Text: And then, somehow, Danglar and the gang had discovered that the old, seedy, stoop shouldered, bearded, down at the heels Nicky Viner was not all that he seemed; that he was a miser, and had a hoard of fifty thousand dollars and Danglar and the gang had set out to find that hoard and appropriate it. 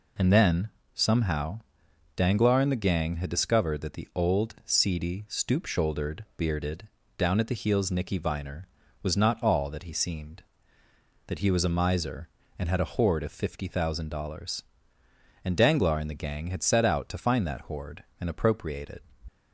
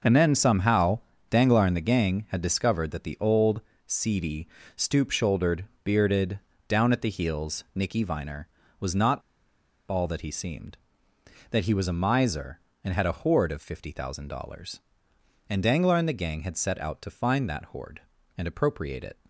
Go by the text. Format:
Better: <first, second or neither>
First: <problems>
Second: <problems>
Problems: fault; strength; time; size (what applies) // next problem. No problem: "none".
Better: first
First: none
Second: starts louder than the rest; noticeable; until 1.3 s; 6 dB // pauses between "not" and "all"; noticeable; at 9.2 s; 0.69 s long